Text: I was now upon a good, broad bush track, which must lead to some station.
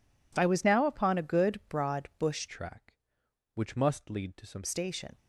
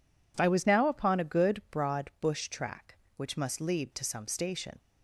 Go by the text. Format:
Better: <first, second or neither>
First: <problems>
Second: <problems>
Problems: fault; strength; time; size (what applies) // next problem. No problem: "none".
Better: second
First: changes voice from "track" to "some"; from 2.4 to 4.6 s; 2.2 s long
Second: none